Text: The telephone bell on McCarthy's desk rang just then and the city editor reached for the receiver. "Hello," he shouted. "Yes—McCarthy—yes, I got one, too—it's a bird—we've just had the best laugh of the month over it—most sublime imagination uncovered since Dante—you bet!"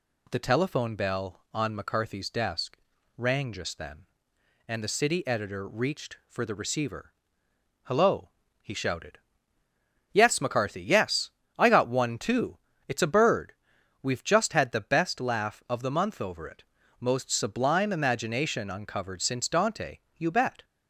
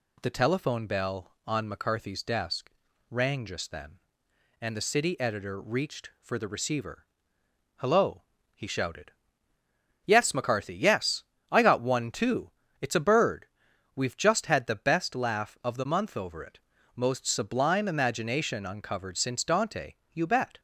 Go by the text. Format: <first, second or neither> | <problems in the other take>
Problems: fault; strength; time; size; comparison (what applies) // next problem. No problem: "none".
neither | pauses between "desk" and "rang"; slight; the same in both